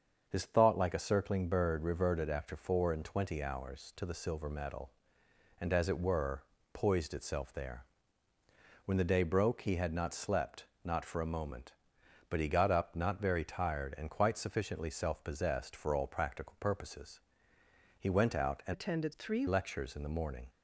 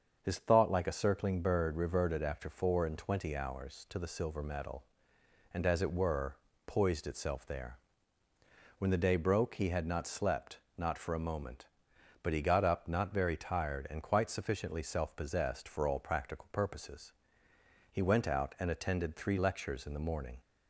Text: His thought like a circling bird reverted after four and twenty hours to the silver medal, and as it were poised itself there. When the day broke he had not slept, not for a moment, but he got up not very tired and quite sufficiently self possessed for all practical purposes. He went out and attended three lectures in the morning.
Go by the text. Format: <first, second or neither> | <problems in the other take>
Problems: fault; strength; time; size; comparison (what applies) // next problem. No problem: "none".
second | starts louder than the rest; until 1.2 s; 6.5 dB; also in the second // pauses between "were" and "poised"; slight; at 6.4 s; 0.30 s long; slight in the second // changes voice from "attended" to "three"; from 18.7 to 19.4 s; 0.7 s long